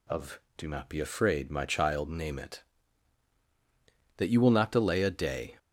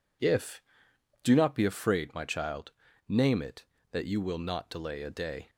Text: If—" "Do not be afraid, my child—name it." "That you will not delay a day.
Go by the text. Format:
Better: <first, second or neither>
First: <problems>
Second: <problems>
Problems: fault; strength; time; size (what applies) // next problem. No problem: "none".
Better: second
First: says "Of" for "If"; at 0.0 s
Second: none